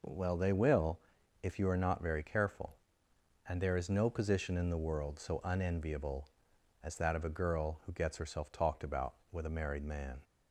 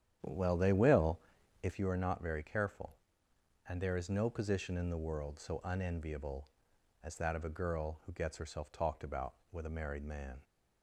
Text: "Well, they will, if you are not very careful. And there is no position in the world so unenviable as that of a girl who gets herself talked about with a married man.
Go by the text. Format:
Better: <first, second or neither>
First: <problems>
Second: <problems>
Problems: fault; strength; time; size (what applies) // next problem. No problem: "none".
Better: first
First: none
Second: starts louder than the rest; strong; until 1.8 s; 9.5 dB